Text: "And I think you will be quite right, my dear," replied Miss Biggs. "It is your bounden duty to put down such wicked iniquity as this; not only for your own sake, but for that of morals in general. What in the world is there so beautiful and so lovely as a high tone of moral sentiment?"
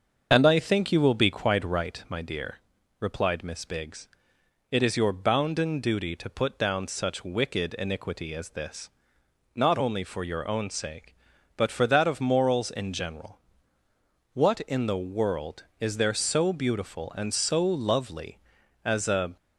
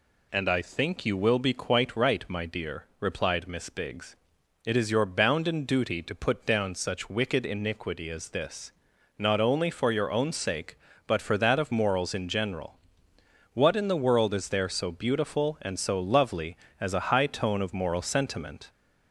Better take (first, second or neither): second